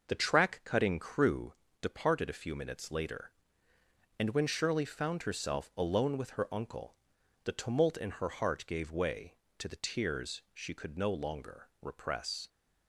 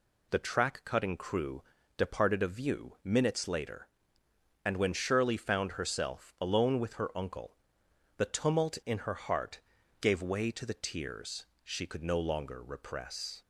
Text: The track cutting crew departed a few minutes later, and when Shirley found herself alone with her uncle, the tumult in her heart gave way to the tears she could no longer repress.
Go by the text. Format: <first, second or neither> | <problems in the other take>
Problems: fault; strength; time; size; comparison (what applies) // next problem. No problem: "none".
first | pauses between "crew" and "departed"; slight; at 1.6 s; 0.34 s long; slight in the first // says "view" for "few"; at 2.4 s // pauses between "heart" and "gave"; at 9.5 s; 0.40 s long // pauses between "tears" and "she"; slight; at 11.4 s; 0.20 s long